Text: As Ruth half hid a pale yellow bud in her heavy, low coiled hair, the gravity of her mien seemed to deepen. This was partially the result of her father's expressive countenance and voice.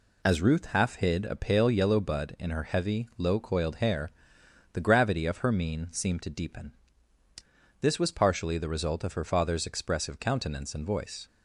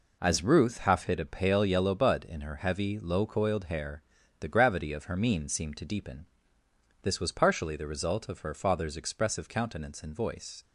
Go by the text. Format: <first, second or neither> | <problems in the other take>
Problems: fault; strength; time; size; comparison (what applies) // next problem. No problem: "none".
neither | none